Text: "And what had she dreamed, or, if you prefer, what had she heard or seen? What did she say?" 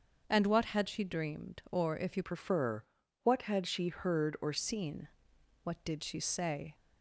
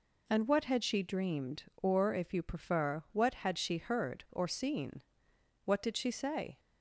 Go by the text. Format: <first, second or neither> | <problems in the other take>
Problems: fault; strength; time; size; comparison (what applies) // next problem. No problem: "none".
second | starts louder than the rest; until 1.2 s; 6.5 dB // changes voice from "prefer" to "or"; from 2.2 to 4.5 s; 2.3 s long